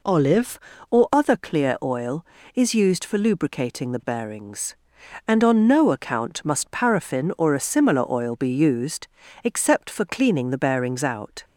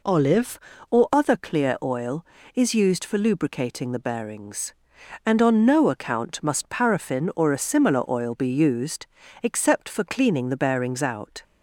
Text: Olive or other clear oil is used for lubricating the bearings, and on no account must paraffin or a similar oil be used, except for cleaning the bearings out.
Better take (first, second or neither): neither